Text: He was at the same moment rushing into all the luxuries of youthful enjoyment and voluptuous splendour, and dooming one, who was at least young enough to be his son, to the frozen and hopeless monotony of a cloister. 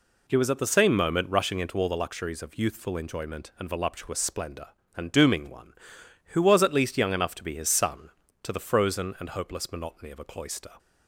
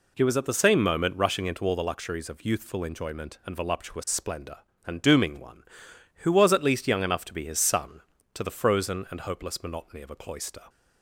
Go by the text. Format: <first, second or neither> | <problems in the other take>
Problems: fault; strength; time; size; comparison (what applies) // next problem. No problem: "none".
neither | none